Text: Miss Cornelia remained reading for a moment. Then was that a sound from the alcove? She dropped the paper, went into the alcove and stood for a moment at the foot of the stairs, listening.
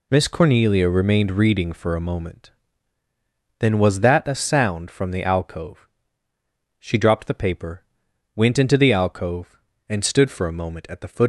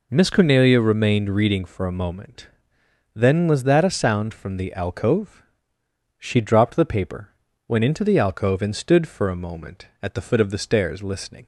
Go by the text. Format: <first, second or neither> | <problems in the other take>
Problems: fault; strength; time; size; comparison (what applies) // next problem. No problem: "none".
second | stops before "of the stairs listening"; at 11.2 s